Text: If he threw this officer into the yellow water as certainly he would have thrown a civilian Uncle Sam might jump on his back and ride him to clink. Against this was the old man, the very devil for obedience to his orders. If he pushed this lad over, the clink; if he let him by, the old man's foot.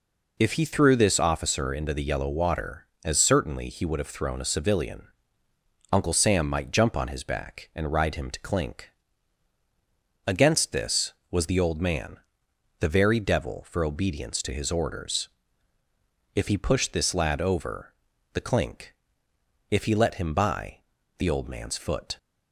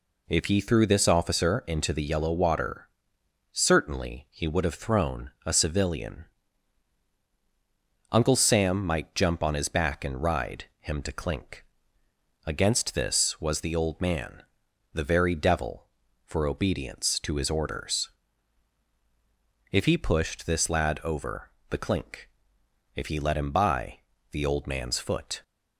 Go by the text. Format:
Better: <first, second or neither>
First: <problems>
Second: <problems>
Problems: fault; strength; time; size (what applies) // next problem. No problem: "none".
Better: first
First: pauses between "civilian" and "Uncle"; noticeable; at 5.0 s; 0.84 s long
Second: skips "as"; at 3.2 s // pauses between "thrown" and "a"; slight; at 5.2 s; 0.16 s long // pauses between "civilian" and "Uncle"; strong; at 6.2 s; 1.8 s long // pauses between "ride" and "him"; slight; at 10.6 s; 0.16 s long